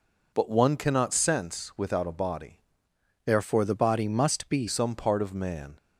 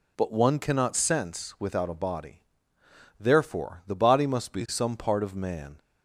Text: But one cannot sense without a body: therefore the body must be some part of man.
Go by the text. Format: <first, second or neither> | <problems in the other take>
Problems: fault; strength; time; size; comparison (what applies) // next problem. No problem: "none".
second | changes voice from "therefore" to "be"; from 3.2 to 4.6 s; 1.4 s long